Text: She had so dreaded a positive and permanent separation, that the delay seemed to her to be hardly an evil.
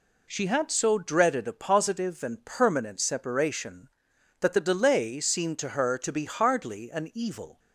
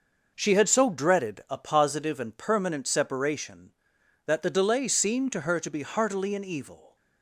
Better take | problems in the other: first | says "heartily" for "hardly"; at 5.8 s

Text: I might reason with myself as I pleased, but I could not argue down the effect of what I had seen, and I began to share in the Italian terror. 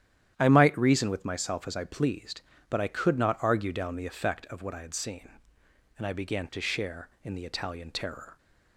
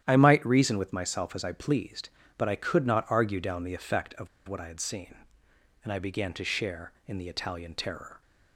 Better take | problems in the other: first | starts louder than the rest; strong; until 1.0 s; 10.5 dB; strong in the first // pauses between "of" and "what"; slight; at 4.2 s; 0.21 s long

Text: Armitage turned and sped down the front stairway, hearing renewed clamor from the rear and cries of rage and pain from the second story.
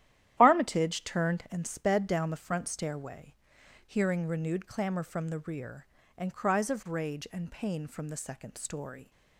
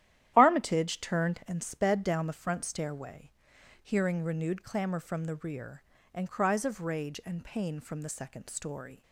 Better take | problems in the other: neither | starts louder than the rest; strong; the same in both

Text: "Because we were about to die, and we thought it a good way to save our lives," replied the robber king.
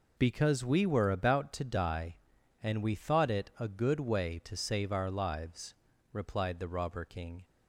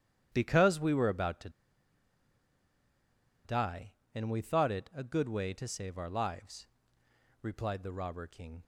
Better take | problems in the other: first | starts louder than the rest; strong; until 1.3 s; 10.5 dB // pauses between "to" and "die"; strong; at 1.4 s; 1.9 s long

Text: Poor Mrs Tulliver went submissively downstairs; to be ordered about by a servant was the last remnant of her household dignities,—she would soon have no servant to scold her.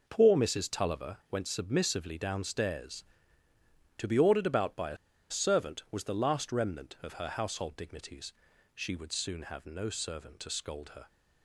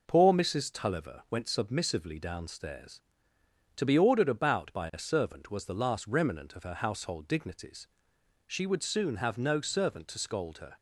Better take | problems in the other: second | pauses between "a" and "servant"; slight; at 4.9 s; 0.33 s long

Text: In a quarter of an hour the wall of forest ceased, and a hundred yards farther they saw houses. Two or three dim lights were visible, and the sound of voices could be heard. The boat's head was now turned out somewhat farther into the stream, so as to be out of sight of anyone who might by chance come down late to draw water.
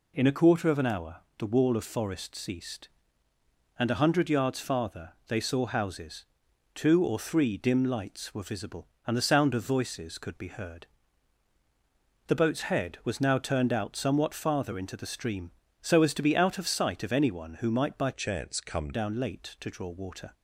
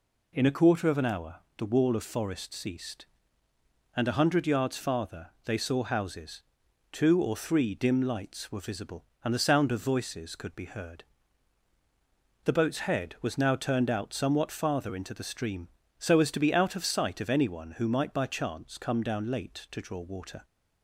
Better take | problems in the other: second | pauses between "hour" and "the"; slight; at 1.1 s; 0.22 s long; slight in the second // pauses between "farther" and "they"; slight; at 5.1 s; 0.16 s long; slight in the second // changes voice from "chance" to "come"; from 18.1 to 18.9 s; 0.8 s long

